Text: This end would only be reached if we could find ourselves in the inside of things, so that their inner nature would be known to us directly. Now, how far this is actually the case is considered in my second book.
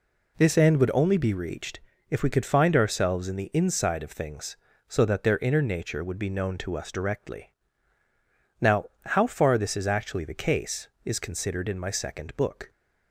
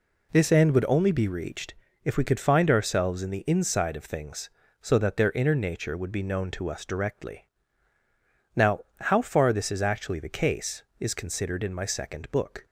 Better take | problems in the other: neither | pauses between "reached" and "if"; slight; the same in both

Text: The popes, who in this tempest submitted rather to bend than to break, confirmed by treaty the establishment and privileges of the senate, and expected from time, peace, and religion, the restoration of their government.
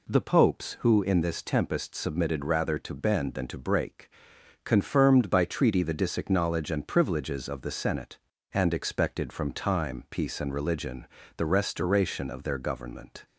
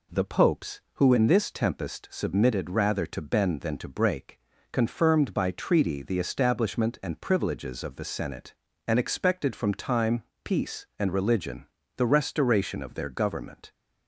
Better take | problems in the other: second | says "disacknowledge" for "establishment"; at 5.9 s

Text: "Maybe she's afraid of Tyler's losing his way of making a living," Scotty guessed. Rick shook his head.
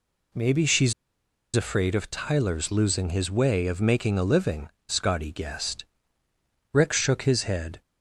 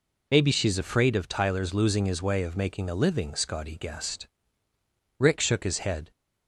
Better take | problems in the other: second | pauses between "she's" and "afraid"; noticeable; at 0.9 s; 0.63 s long

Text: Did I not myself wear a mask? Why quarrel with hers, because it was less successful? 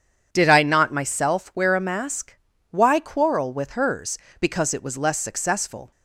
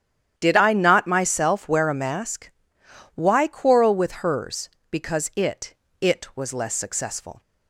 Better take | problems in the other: first | starts louder than the rest; strong; until 1.3 s; 10 dB // says "it" twice; at 6.0 s

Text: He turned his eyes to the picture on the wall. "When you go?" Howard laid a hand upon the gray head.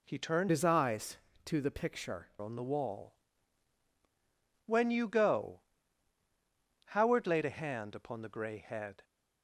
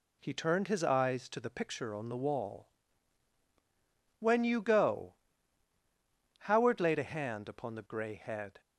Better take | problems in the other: second | changes voice from "his" to "picture"; from 0.4 to 2.2 s; 1.8 s long

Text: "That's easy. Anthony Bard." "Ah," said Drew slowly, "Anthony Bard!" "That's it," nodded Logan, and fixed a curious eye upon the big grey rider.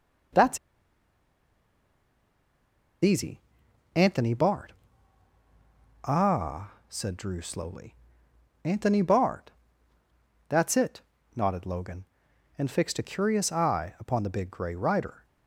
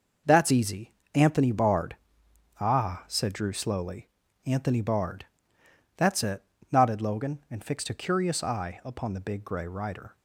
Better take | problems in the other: second | pauses between "That's" and "easy"; strong; at 0.5 s; 2.4 s long

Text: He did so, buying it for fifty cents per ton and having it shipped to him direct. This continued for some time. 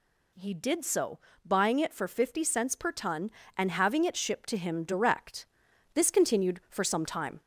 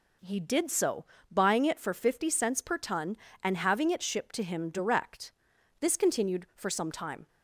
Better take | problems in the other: second | gets louder; slight; throughout; 2 dB

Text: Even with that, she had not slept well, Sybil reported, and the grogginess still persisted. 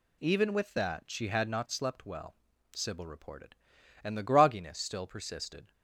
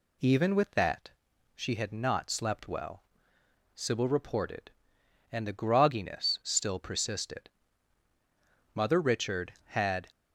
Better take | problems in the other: first | goes on to say "Mother Richard had"; from 8.7 s on; 1.3 s long

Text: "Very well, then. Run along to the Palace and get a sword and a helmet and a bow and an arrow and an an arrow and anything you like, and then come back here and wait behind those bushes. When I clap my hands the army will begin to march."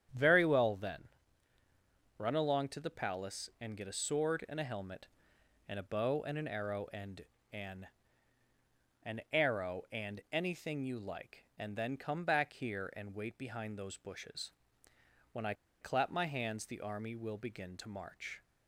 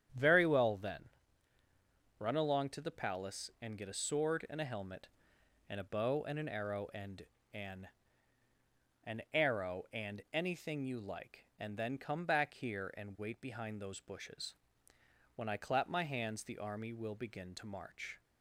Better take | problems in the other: second | starts louder than the rest; strong; until 2.2 s; 9 dB; strong in the second // pauses between "and" and "an"; slight; at 7.2 s; 0.28 s long; slight in the second // pauses between "an" and "an"; at 7.8 s; 1.1 s long; also in the second // pauses between "I" and "clap"; slight; at 15.5 s; 0.27 s long

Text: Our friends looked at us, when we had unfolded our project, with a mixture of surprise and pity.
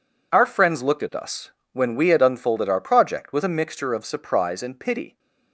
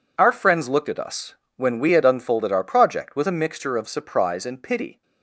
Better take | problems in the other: neither | none

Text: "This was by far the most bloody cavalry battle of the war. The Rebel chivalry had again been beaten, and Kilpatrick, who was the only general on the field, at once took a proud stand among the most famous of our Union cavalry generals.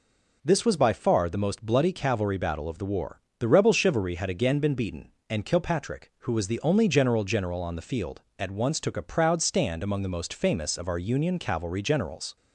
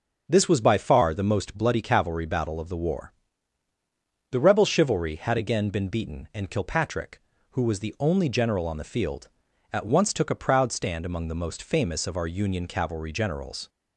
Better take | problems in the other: second | says "general" twice; at 7.2 s

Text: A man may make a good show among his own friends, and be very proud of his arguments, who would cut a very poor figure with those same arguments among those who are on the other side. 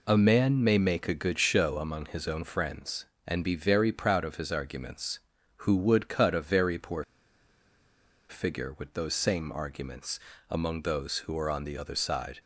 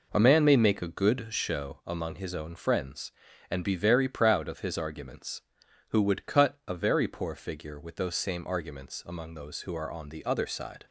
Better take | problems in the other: second | pauses between "poor" and "figure"; strong; at 7.0 s; 1.2 s long // pauses between "arguments" and "among"; slight; at 10.2 s; 0.28 s long

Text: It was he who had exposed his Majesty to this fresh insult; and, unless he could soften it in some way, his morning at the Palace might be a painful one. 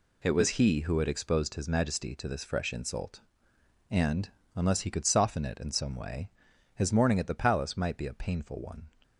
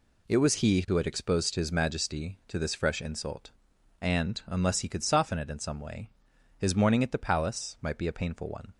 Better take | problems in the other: neither | none

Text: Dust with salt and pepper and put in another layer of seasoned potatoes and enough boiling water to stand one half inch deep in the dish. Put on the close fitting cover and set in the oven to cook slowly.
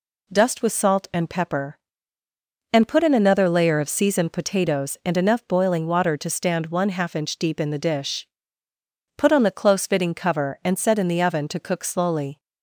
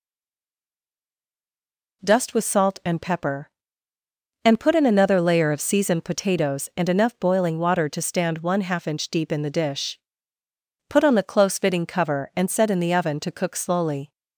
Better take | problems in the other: first | stays silent before the first word; noticeable; until 2.0 s; 2.0 s long

